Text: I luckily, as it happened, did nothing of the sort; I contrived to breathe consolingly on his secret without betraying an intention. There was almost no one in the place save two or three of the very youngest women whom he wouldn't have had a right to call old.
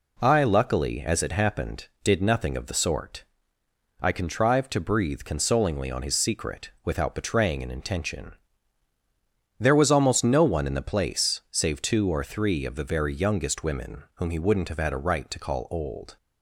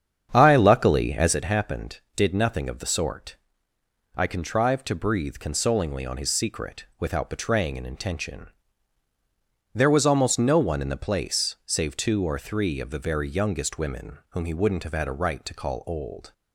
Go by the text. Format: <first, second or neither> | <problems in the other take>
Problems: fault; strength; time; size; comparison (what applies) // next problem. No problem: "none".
first | starts louder than the rest; strong; until 1.5 s; 8 dB